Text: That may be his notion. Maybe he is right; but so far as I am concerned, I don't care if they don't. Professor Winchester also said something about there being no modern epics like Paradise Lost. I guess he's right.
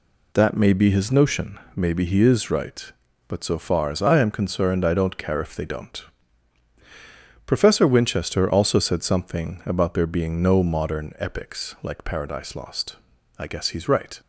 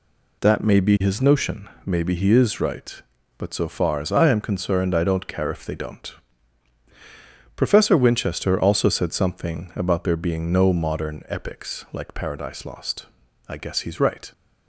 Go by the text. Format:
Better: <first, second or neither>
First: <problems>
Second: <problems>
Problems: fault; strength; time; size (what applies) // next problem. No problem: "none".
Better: neither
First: none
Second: none